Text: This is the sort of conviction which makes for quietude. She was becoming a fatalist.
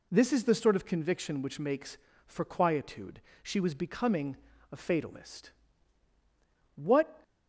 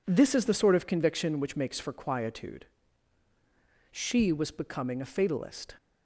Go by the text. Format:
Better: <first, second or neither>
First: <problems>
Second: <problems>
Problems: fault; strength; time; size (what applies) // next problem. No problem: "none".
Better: second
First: pauses between "becoming" and "a"; slight; at 4.3 s; 0.34 s long // goes on to say "What"; slight; from 6.7 s on; 0.48 s long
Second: none